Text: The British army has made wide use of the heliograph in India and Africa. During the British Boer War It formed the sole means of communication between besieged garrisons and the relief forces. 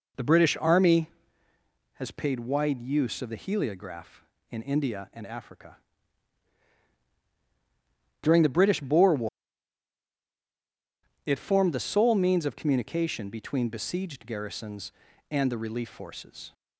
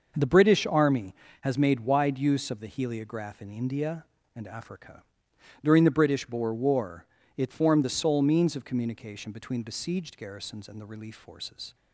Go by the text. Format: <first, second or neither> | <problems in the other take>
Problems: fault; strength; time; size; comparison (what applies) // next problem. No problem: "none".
second | says "paid" for "made"; at 2.1 s // pauses between "War" and "It"; strong; at 9.2 s; 1.9 s long; slight in the second